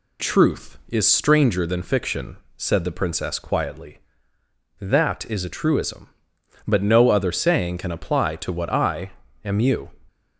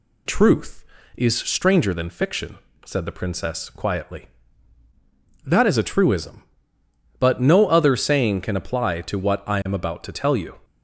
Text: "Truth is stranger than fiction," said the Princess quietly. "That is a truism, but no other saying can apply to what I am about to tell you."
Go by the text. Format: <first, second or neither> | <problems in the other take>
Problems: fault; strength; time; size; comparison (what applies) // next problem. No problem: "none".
second | pauses between "I" and "am"; slight; at 9.1 s; 0.34 s long // skips "about to tell"; at 9.5 s